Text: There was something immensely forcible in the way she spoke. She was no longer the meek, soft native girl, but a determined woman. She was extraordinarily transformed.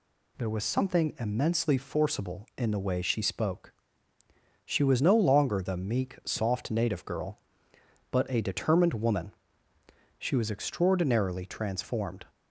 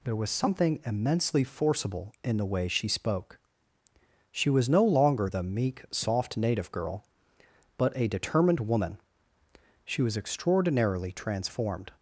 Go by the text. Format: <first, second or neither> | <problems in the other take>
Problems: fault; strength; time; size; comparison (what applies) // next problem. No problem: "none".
neither | none